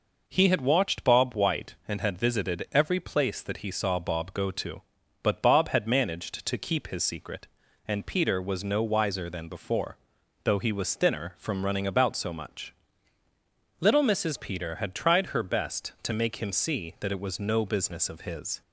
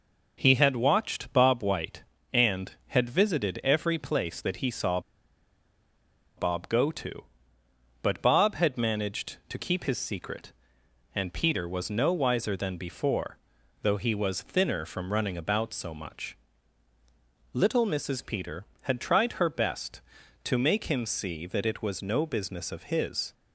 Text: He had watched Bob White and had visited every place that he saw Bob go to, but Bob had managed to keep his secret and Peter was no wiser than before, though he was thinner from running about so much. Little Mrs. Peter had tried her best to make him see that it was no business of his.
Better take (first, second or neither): first